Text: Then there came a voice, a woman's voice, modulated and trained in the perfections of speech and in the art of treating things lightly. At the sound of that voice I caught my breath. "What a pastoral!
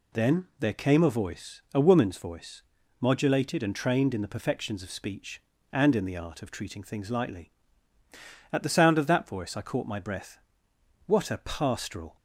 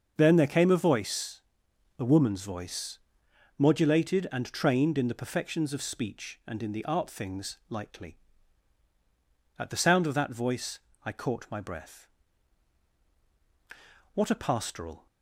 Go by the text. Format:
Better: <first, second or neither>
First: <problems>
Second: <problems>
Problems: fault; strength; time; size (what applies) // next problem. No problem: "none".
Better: first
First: none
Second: starts louder than the rest; until 1.1 s; 6.5 dB // skips "of treating"; at 7.0 s // pauses between "voice" and "I"; slight; at 10.7 s; 0.24 s long